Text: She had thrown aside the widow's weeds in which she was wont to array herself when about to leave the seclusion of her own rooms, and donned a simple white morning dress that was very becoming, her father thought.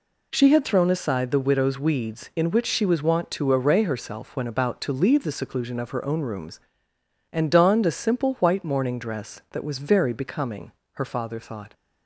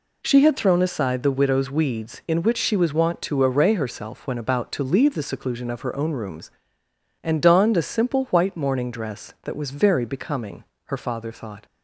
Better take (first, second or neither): neither